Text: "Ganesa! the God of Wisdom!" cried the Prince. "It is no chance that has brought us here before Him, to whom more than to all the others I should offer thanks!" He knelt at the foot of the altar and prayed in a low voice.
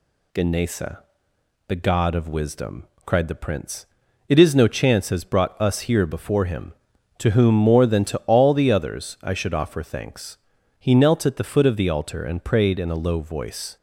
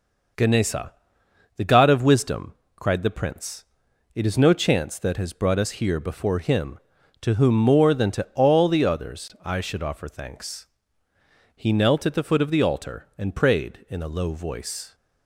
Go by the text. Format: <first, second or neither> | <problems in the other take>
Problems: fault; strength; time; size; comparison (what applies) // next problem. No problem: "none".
second | skips "that"; at 5.0 s